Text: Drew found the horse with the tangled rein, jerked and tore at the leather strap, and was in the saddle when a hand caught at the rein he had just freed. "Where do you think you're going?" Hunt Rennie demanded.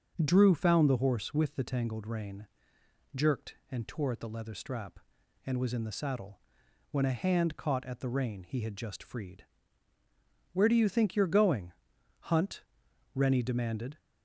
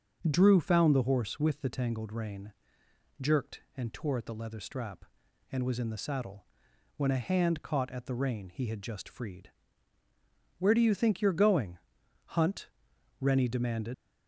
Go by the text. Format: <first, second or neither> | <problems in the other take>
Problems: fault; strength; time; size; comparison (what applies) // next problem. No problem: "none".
first | starts louder than the rest; until 1.2 s; 6.5 dB; also in the first // pauses between "saddle" and "when"; noticeable; at 6.4 s; 0.52 s long; noticeable in the first // pauses between "Hunt" and "Rennie"; noticeable; at 12.6 s; 0.50 s long; noticeable in the first // leaves "demanded" unfinished; at 13.9 s; 85 ms